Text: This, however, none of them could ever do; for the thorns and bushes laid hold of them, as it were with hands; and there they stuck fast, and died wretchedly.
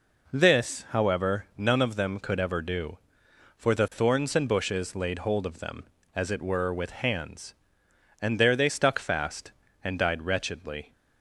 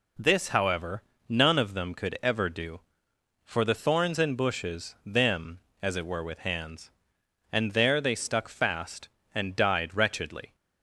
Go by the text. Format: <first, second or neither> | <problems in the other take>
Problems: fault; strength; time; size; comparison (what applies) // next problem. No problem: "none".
first | skips "laid hold of"; at 4.9 s